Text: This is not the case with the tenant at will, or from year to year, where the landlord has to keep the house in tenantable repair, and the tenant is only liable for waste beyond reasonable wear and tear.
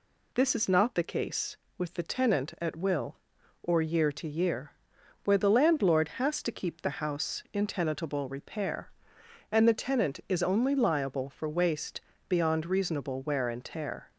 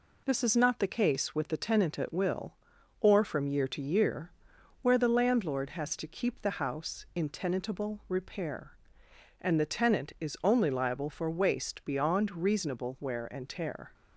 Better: second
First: skips "from"; at 3.8 s // pauses between "waste" and "beyond"; slight; at 12.0 s; 0.26 s long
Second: none

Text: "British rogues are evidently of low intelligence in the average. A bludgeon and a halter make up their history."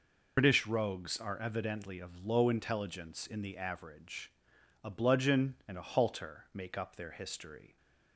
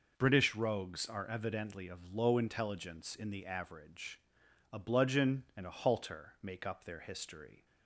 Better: second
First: loses the start of "British"; at 0.3 s; 90 ms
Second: none

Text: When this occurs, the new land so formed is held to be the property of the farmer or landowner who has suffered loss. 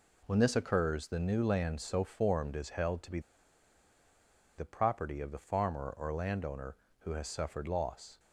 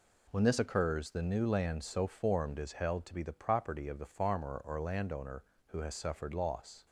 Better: second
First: pauses between "be" and "the"; strong; at 3.1 s; 1.3 s long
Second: none

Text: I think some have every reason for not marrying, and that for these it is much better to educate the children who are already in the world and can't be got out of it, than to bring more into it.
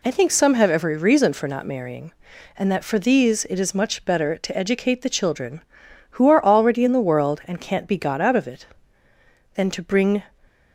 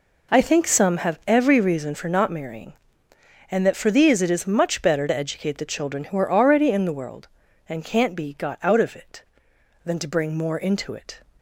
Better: second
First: stops before "more into it"; at 10.4 s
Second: none

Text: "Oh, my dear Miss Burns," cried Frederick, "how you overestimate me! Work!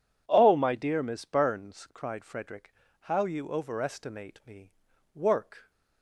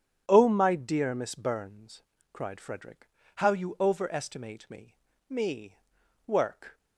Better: first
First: none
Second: starts louder than the rest; strong; until 1.2 s; 8.5 dB // says "me" twice; at 5.2 s

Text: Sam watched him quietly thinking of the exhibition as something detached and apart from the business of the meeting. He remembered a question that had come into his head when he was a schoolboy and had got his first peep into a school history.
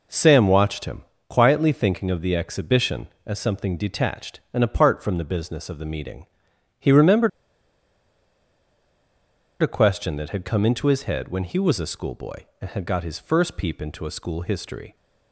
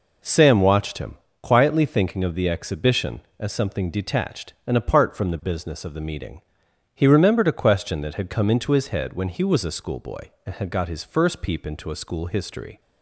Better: second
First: pauses between "him" and "quietly"; slight; at 1.0 s; 0.26 s long // pauses between "remembered" and "a"; strong; at 7.2 s; 2.3 s long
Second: pauses between "him" and "quietly"; slight; at 1.1 s; 0.26 s long

